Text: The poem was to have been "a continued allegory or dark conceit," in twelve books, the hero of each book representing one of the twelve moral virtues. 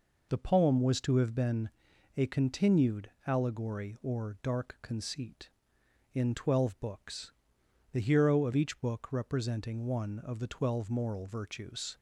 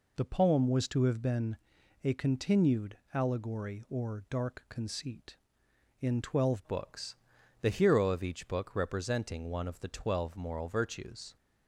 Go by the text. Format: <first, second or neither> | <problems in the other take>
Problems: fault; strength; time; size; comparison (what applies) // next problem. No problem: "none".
first | pauses between "been" and "a"; noticeable; at 1.5 s; 0.48 s long; noticeable in the first // pauses between "continued" and "allegory"; slight; at 2.9 s; 0.16 s long; slight in the first // changes voice at "books"; from 6.6 s on; 4.7 s long